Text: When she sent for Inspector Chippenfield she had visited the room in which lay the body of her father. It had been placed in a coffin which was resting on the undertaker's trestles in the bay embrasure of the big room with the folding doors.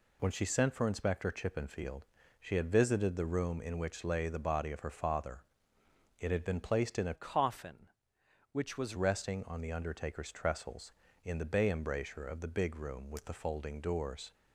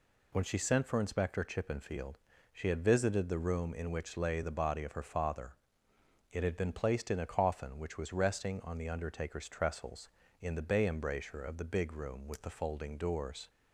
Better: second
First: pauses between "Chippenfield" and "she"; slight; at 2.0 s; 0.36 s long // changes voice from "coffin" to "was"; from 7.1 to 8.9 s; 1.8 s long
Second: pauses between "Chippenfield" and "she"; slight; at 2.1 s; 0.36 s long

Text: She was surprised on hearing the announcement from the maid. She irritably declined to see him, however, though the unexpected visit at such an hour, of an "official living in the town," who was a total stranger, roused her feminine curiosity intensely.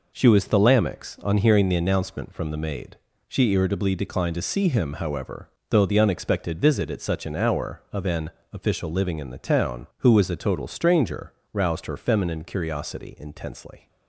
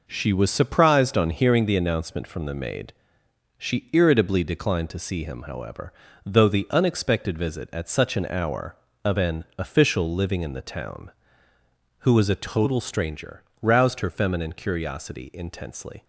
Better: second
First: says "thalamics" for "surprised"; at 0.4 s // pauses between "an" and "official"; slight; at 8.2 s; 0.24 s long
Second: none

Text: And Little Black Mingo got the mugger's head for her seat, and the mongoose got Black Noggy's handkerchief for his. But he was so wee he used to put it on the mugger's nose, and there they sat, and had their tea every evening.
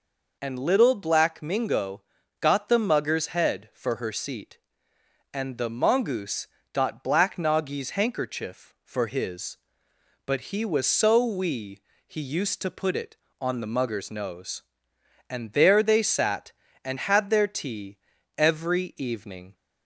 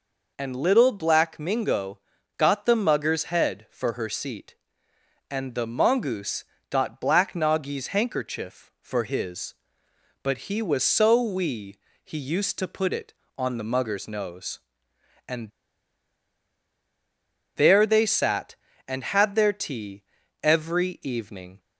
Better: first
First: pauses between "Mingo" and "got"; at 2.0 s; 0.38 s long // pauses between "mongoose" and "got"; slight; at 6.4 s; 0.26 s long // pauses between "wee" and "he"; slight; at 11.7 s; 0.28 s long // pauses between "tea" and "every"; at 17.9 s; 0.40 s long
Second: pauses between "Mingo" and "got"; at 1.9 s; 0.38 s long // pauses between "mongoose" and "got"; slight; at 6.4 s; 0.26 s long // pauses between "wee" and "he"; slight; at 11.7 s; 0.28 s long // pauses between "and" and "there"; strong; at 15.5 s; 2.0 s long // pauses between "tea" and "every"; at 20.0 s; 0.40 s long

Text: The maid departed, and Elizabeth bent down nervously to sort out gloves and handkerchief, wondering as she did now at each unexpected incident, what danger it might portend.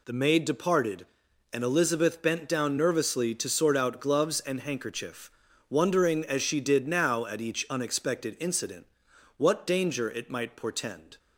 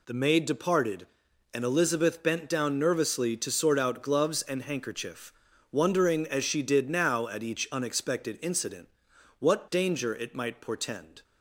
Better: neither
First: none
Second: none

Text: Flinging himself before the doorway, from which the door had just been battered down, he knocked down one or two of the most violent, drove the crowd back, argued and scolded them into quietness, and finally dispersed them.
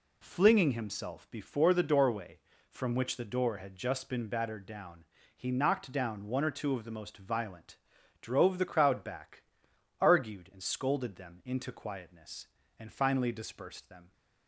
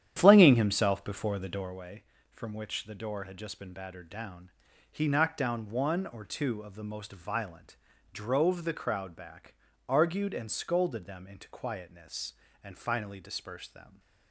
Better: first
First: none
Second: starts louder than the rest; strong; until 1.8 s; 10 dB

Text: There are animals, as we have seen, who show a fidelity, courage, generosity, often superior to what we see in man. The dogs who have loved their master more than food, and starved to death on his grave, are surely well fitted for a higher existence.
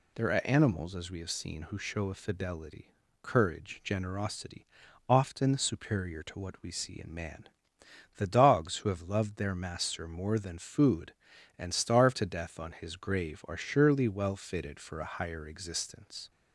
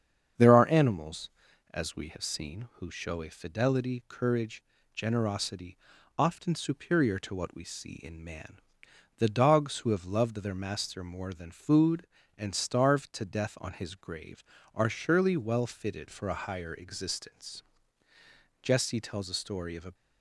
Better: first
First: none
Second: starts louder than the rest; strong; until 1.8 s; 7.5 dB // goes on to say "Jesse tells a story of a"; from 18.6 s on; 1.3 s long

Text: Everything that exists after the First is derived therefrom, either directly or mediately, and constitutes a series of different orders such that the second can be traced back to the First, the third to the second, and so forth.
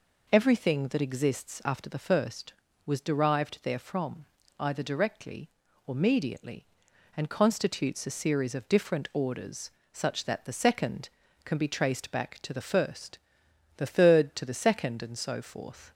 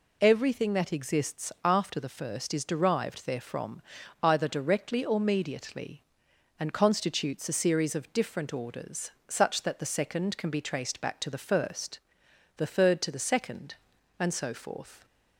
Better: second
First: says "was" for "is"; at 2.8 s // pauses between "orders" and "such"; slight; at 9.6 s; 0.24 s long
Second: pauses between "orders" and "such"; slight; at 9.1 s; 0.16 s long

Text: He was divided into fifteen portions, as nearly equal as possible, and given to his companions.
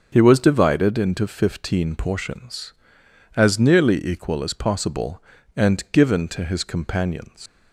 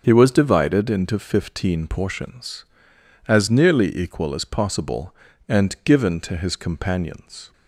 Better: second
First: starts louder than the rest; until 1.1 s; 6 dB // leaves "companions" unfinished; at 7.4 s; 140 ms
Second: starts louder than the rest; until 1.0 s; 6.5 dB

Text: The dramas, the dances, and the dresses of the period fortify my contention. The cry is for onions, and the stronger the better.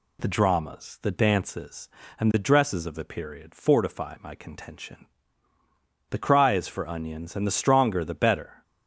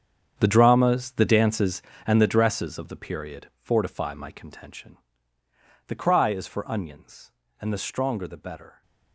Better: first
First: none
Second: gets quieter; strong; throughout; 14 dB

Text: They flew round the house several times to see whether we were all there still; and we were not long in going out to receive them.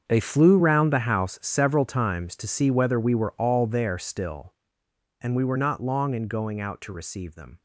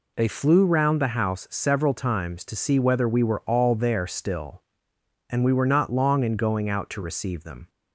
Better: second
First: gets quieter; strong; throughout; 15 dB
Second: none

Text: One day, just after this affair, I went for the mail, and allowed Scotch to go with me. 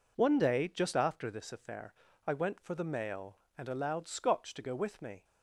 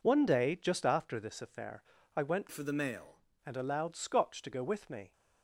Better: first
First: none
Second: changes voice from "for" to "mail"; from 2.5 to 3.1 s; 0.6 s long

